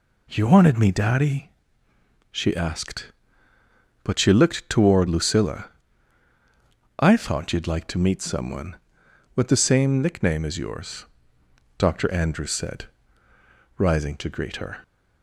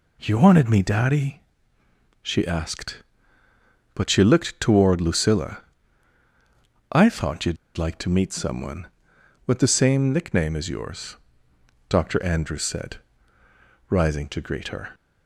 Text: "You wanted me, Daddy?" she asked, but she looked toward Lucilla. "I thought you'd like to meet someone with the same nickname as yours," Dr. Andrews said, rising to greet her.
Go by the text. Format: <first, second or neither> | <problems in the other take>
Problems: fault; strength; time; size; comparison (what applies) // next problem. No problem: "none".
first | pauses between "you'd" and "like"; slight; at 7.5 s; 0.21 s long